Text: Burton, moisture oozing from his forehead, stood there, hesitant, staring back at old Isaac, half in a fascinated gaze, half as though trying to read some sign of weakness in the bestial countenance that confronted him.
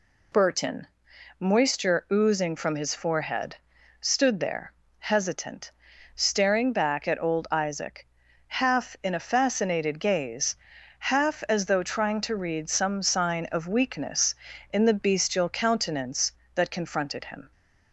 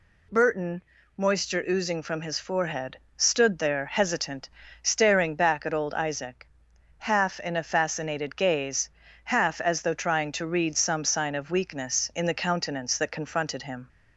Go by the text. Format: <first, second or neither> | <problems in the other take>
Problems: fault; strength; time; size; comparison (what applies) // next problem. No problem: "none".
first | skips "bestial"; at 12.3 s